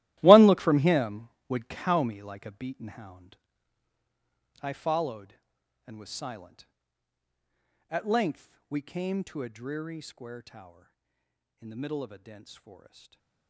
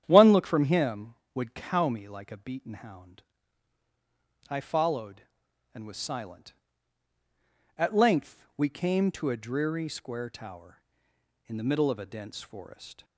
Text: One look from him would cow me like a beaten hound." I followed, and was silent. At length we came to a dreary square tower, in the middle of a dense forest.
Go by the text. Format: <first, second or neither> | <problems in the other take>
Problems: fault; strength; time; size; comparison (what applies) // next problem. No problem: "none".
second | gets quieter; strong; throughout; 15 dB // starts louder than the rest; strong; until 1.2 s; 15.5 dB; strong in the second // stays silent after the last word; slight; from 12.7 s on; 0.7 s long